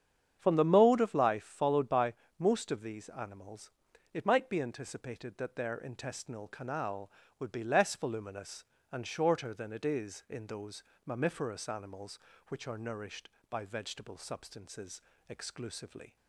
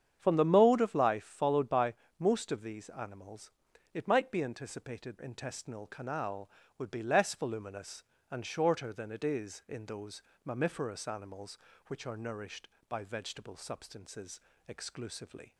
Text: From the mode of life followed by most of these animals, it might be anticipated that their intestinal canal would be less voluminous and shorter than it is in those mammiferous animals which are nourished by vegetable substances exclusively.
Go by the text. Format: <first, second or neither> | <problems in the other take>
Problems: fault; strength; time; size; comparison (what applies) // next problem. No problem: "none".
first | starts louder than the rest; strong; until 1.2 s; 8.5 dB; strong in the first // pauses between "by" and "most"; slight; at 1.9 s; 0.24 s long; slight in the first // skips "that their"; at 5.1 s // pauses between "those" and "mammiferous"; slight; at 10.2 s; 0.22 s long; slight in the first // pauses between "substances" and "exclusively"; slight; at 14.3 s; 0.28 s long; slight in the first